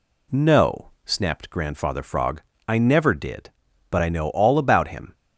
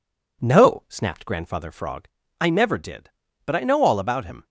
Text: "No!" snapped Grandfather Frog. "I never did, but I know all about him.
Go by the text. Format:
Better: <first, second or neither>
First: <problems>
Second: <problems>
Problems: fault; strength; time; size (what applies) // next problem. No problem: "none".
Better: neither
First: none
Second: none